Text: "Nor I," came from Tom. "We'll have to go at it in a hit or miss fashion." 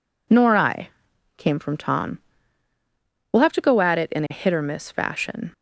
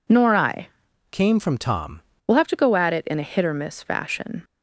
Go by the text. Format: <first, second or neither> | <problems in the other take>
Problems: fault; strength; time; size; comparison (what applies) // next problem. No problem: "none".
first | changes voice from "came" to "Tom"; from 1.1 to 1.9 s; 0.8 s long